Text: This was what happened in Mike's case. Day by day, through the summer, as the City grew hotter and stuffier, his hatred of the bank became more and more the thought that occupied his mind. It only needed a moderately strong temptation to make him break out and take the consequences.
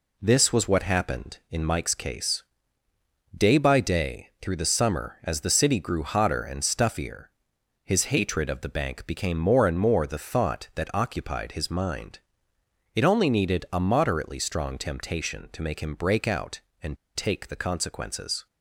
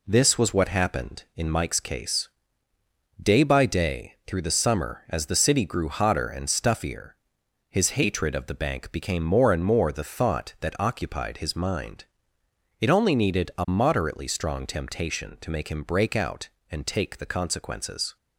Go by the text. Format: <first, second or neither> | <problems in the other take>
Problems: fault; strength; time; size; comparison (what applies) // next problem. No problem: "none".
second | pauses between "and" and "take"; slight; at 16.9 s; 0.19 s long